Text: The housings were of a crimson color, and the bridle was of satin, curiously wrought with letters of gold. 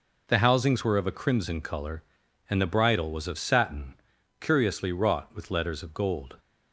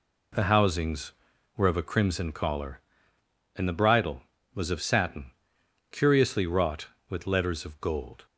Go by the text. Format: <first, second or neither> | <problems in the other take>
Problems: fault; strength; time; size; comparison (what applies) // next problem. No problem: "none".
first | says "collar" for "color"; at 2.3 s